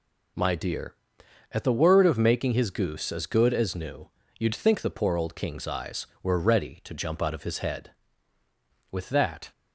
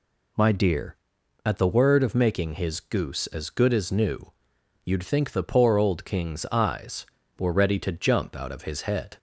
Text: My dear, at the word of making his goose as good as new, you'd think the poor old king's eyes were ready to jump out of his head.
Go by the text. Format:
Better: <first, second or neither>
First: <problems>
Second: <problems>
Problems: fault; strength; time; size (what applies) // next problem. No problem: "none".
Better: second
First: goes on to say "With that"; from 8.9 s on; 0.60 s long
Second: none